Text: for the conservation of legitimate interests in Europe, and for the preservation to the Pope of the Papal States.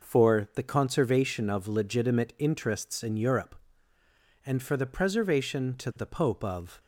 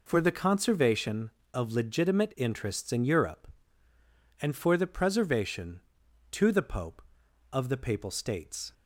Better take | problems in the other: second | stops before "the Papal States"; at 6.7 s

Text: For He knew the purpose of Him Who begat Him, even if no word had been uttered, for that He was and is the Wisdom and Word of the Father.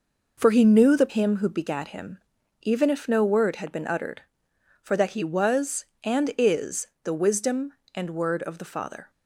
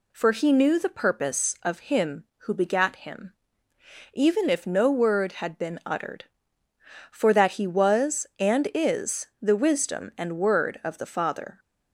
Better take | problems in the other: second | skips "purpose of"; at 1.0 s // pauses between "is" and "the"; slight; at 6.8 s; 0.18 s long

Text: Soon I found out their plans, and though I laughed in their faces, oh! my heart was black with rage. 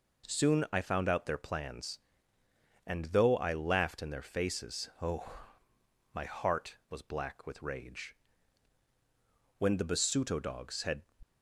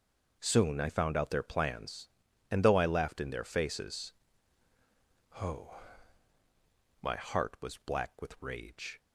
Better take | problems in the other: second | goes on to say "When the Basuto dogs had"; from 9.5 s on; 1.4 s long

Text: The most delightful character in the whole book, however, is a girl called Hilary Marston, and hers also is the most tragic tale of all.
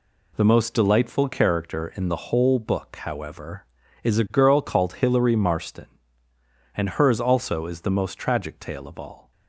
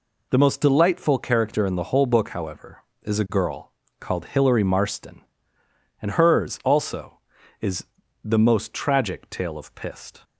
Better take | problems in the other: first | pauses between "girl" and "called"; slight; at 3.7 s; 0.28 s long // pauses between "is" and "the"; at 7.8 s; 0.38 s long // says "pist" for "all"; at 9.7 s

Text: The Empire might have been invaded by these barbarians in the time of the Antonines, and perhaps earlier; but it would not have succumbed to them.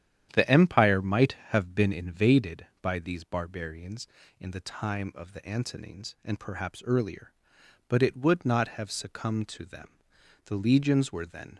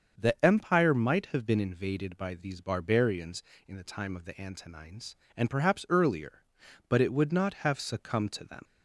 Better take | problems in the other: second | starts louder than the rest; strong; until 1.3 s; 10 dB; also in the second // goes on to say "The Legions were then"; noticeable; from 10.4 s on; 1.1 s long

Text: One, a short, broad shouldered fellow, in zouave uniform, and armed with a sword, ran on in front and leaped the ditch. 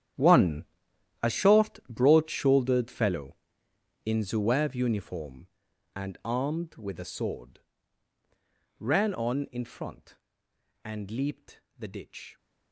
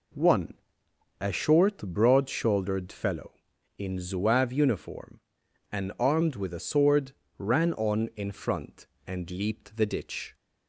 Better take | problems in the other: second | gets quieter; strong; throughout; 16.5 dB // pauses between "leaped" and "the"; slight; at 11.6 s; 0.18 s long

